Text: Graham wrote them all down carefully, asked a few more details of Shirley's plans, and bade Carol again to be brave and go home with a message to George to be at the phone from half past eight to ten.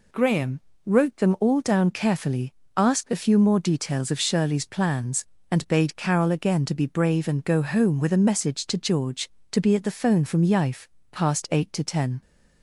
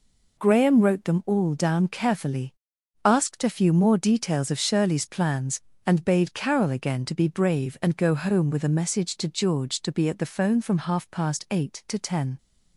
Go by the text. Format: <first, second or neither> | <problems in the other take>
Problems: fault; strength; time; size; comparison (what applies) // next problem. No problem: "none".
second | pauses between "Graham" and "wrote"; slight; at 0.6 s; 0.24 s long // says "yife" for "half"; at 10.4 s